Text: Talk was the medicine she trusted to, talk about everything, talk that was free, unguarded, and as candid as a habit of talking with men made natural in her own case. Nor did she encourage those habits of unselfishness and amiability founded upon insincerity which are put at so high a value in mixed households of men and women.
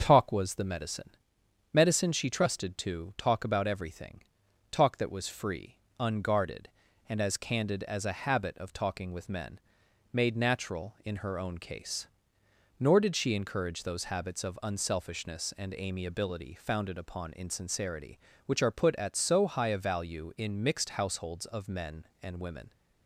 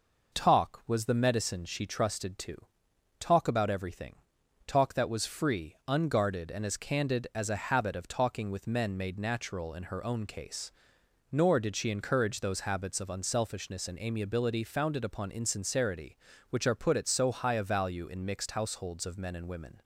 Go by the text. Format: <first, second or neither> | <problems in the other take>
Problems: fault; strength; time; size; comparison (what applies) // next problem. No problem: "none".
second | starts louder than the rest; until 1.0 s; 6.5 dB // says "medicine" twice; at 1.7 s // pauses between "men" and "made"; noticeable; at 9.5 s; 0.52 s long